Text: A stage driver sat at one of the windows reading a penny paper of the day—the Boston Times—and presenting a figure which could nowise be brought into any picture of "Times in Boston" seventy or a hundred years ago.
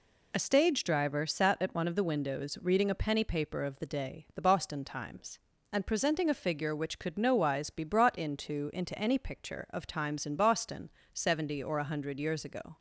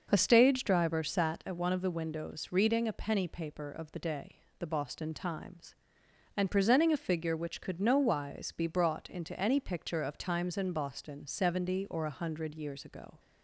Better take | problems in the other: second | says "into" twice; at 8.7 s // pauses between "Boston" and "seventy"; slight; at 10.8 s; 0.22 s long

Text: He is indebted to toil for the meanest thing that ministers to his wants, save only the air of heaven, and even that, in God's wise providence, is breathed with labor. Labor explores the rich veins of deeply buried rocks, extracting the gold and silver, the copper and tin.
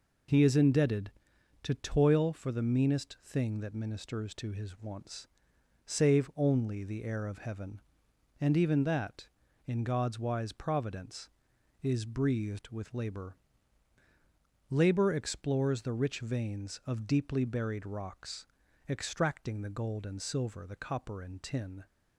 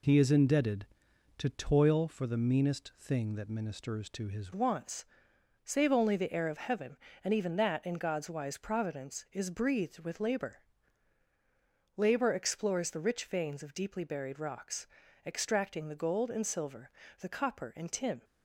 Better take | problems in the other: first | changes voice at "wants"; from 4.5 s on; 13.7 s long

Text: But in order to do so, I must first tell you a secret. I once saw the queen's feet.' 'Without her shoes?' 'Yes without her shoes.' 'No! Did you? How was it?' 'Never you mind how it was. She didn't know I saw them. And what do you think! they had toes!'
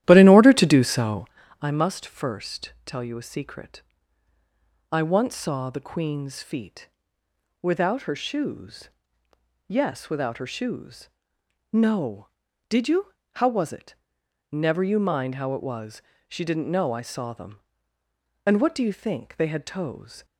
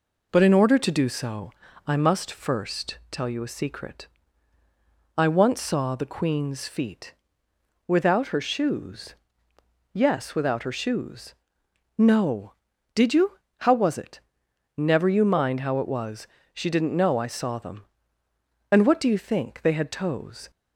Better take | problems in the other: second | starts louder than the rest; strong; until 1.4 s; 13 dB

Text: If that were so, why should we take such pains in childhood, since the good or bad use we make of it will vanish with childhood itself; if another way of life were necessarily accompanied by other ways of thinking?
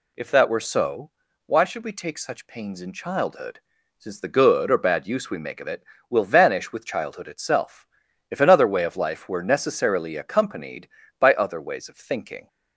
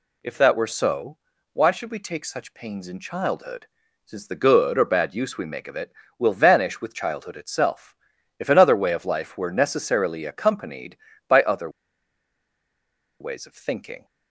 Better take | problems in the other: first | pauses between "other" and "ways"; strong; at 11.7 s; 1.5 s long

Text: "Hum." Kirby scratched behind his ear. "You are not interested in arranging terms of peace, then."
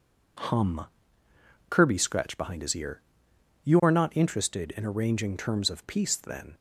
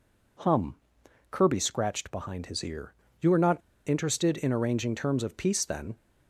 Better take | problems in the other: first | pauses between "not" and "interested"; slight; at 3.6 s; 0.28 s long

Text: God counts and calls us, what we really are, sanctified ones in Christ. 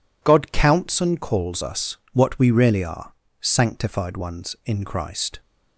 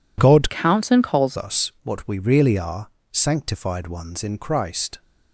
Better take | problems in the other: first | changes voice from "counts" to "calls"; from 0.4 to 1.3 s; 0.9 s long

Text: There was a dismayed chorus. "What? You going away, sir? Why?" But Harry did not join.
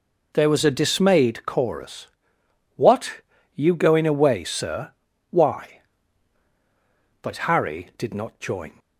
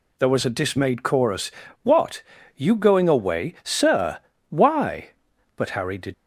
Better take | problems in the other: first | stops before "not join"; at 6.1 s

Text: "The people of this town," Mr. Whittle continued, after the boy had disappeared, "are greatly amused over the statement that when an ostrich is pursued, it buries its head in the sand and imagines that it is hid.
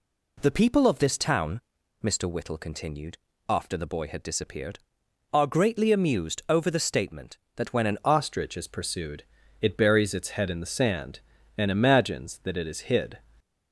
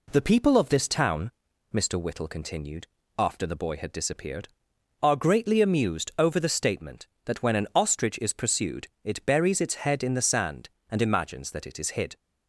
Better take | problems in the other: second | changes voice at "ostrich"; from 8.0 s on; 5.1 s long

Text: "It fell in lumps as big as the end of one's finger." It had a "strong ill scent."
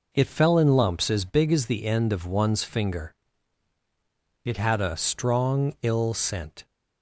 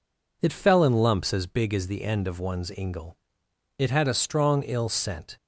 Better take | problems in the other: first | says "ingle" for "finger"; at 2.7 s

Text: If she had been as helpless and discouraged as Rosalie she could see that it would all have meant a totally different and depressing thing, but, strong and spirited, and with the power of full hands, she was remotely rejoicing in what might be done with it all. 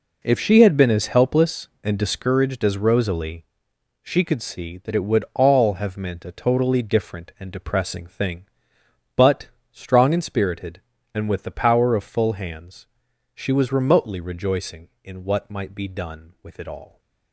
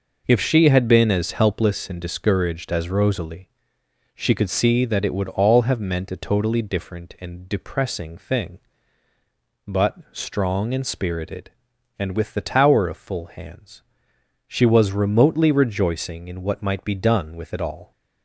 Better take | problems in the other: first | pauses between "Rosalie" and "she"; noticeable; at 3.4 s; 0.68 s long; noticeable in the first // says "tower" for "power"; at 12.3 s

